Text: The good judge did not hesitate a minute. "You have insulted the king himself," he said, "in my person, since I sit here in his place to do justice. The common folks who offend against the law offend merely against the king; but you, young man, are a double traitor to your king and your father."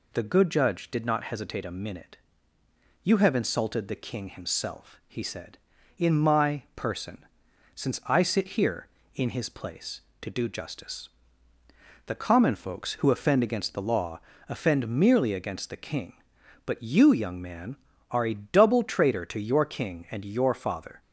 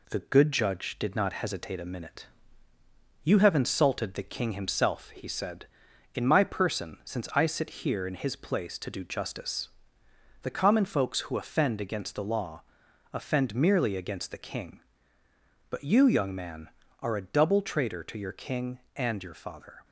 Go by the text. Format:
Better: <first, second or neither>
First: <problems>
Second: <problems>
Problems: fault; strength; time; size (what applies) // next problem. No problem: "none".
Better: first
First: pauses between "law" and "offend"; slight; at 14.1 s; 0.30 s long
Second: gets quieter; slight; throughout; 2.5 dB // pauses between "law" and "offend"; noticeable; at 12.6 s; 0.54 s long